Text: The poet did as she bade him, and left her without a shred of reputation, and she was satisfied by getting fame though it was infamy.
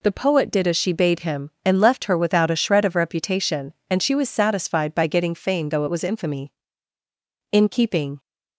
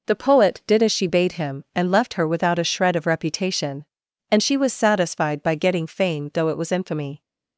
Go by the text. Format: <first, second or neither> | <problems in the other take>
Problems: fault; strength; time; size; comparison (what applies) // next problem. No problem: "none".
second | goes on to say "In keeping"; noticeable; from 7.5 s on; 0.68 s long